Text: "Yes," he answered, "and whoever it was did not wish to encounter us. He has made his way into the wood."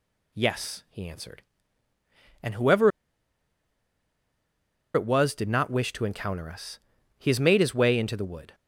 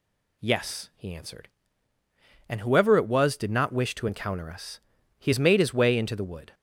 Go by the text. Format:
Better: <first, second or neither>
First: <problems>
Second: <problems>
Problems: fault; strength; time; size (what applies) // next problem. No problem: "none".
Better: second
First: pauses between "whoever" and "it"; strong; at 2.9 s; 2.0 s long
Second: none